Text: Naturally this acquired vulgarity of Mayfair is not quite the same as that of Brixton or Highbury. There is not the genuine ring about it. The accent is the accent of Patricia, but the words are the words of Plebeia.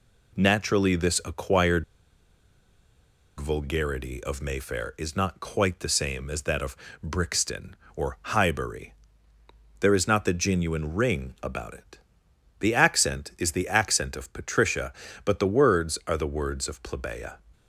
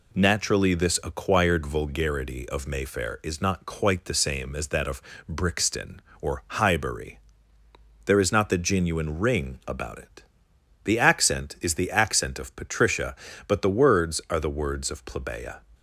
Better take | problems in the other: second | pauses between "acquired" and "vulgarity"; strong; at 1.8 s; 1.5 s long // pauses between "of" and "Brixton"; slight; at 6.7 s; 0.28 s long; slight in the second

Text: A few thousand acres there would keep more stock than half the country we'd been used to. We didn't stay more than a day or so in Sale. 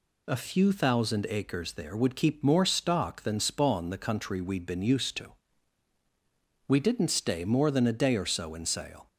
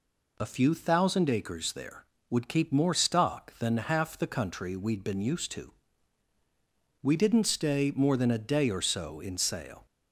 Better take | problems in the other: second | says "spawn" for "half"; at 3.3 s

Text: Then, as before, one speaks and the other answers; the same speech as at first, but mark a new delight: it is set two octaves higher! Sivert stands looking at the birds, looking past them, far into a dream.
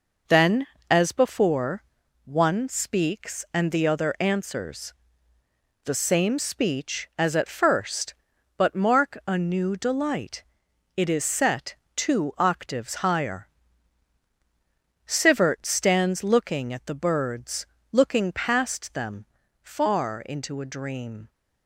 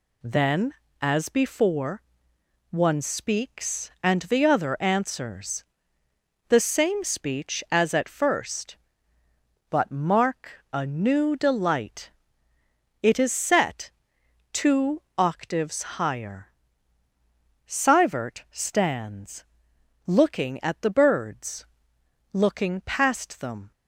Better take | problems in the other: first | pauses between "set" and "two"; noticeable; at 13.9 s; 0.62 s long; slight in the first // pauses between "two" and "octaves"; slight; at 15.0 s; 0.16 s long // pauses between "stands" and "looking"; noticeable; at 19.4 s; 0.64 s long // stops before "far into a dream"; at 23.7 s

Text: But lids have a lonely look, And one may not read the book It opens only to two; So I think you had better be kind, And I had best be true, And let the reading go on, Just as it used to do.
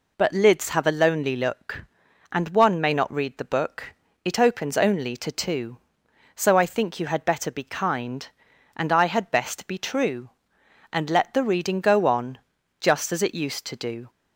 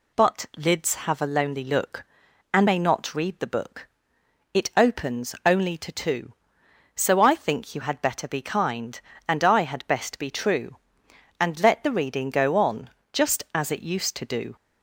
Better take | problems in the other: first | skips "one"; at 2.6 s // pauses between "book" and "It"; noticeable; at 3.8 s; 0.66 s long; slight in the first

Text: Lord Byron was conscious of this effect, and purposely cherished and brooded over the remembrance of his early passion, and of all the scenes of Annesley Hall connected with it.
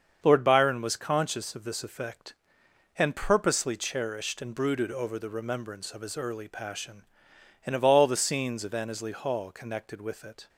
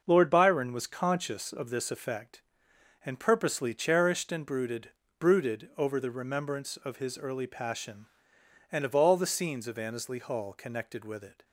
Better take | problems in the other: first | starts louder than the rest; noticeable; until 1.0 s; 6 dB; also in the first // says "brooded" twice; at 5.2 s

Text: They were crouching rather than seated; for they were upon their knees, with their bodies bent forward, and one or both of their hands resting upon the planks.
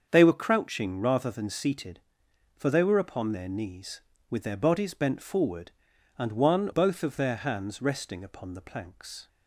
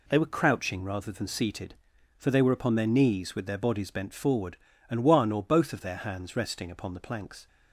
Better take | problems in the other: second | starts louder than the rest; until 1.1 s; 7 dB // skips "or"; at 6.7 s

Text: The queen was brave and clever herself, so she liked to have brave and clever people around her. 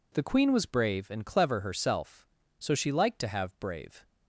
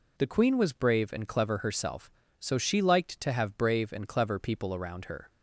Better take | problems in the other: second | stops before "and clever people around her"; at 4.0 s

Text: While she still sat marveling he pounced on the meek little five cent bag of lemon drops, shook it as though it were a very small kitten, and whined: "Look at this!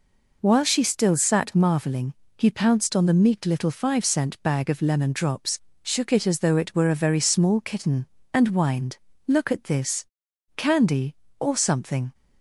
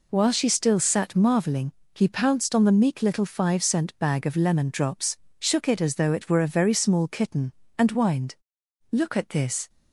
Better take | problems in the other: second | pauses between "marveling" and "he"; slight; at 2.1 s; 0.24 s long; slight in the second // goes on to say "Candy or something"; from 10.5 s on; 1.5 s long

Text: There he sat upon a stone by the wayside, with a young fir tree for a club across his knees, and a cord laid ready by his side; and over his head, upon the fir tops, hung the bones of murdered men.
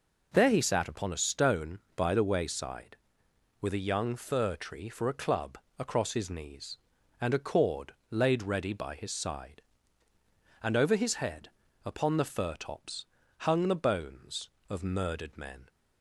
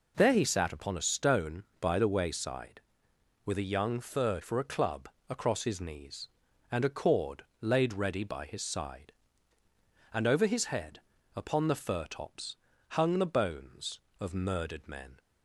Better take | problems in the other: first | skips "tree"; at 4.4 s // pauses between "club" and "across"; slight; at 5.0 s; 0.20 s long; slight in the first // pauses between "cord" and "laid"; slight; at 7.4 s; 0.18 s long; slight in the first

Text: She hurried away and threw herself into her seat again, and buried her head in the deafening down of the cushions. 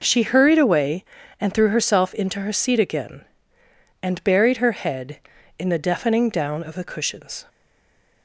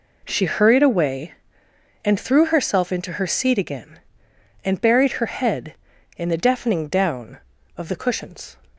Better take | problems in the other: second | stays silent after the last word; slight; from 7.4 s on; 0.8 s long

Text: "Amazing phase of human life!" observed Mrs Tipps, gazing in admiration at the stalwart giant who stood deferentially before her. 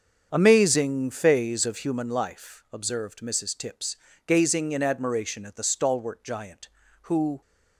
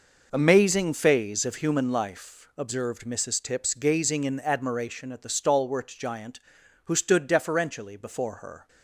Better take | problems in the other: second | starts louder than the rest; strong; until 1.3 s; 7 dB // stops before "stood deferentially before her"; at 7.4 s

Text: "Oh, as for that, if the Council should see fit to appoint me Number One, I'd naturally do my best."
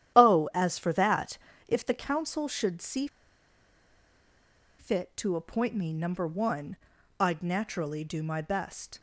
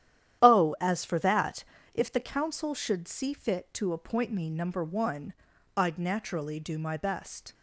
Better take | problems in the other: second | starts louder than the rest; strong; until 1.2 s; 11 dB; strong in the second // pauses between "see" and "fit"; strong; at 3.0 s; 1.7 s long

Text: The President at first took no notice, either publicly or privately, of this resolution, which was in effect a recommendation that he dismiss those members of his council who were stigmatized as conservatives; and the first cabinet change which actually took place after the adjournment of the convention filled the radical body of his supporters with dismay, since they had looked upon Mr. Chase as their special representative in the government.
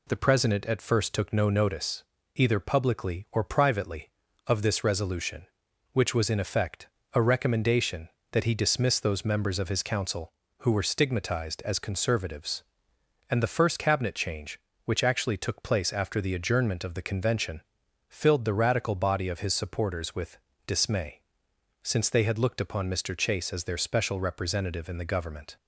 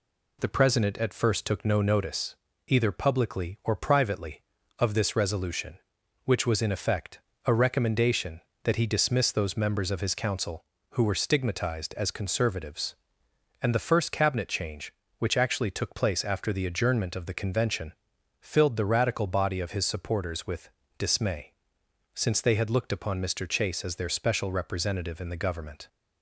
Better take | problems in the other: neither | pauses between "effect" and "a"; slight; the same in both // pauses between "convention" and "filled"; noticeable; the same in both // pauses between "with" and "dismay"; slight; the same in both

